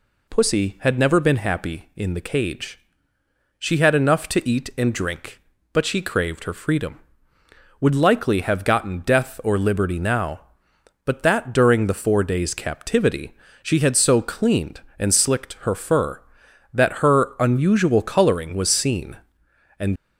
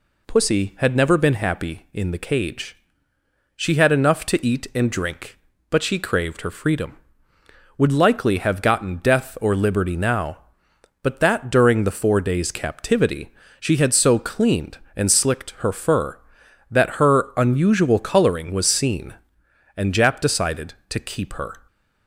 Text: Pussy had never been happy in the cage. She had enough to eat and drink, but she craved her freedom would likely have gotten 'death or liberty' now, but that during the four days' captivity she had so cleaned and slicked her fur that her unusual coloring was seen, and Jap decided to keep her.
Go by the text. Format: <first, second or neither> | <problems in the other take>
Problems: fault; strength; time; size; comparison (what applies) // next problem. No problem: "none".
second | pauses between "captivity" and "she"; slight; at 13.3 s; 0.26 s long; slight in the second // stops before "Jap decided to keep her"; at 19.9 s